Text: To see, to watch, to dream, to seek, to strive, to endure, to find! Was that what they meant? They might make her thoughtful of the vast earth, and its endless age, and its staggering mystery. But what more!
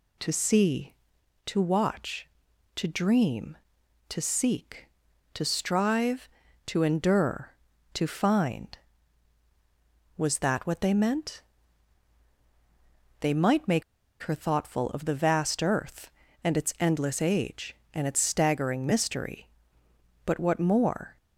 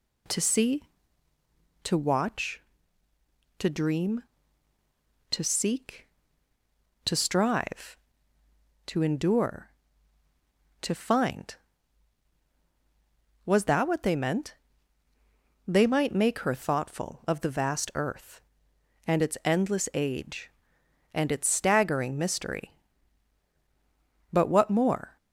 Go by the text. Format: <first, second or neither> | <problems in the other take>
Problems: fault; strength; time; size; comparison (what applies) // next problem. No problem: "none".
second | pauses between "make" and "her"; at 13.8 s; 0.39 s long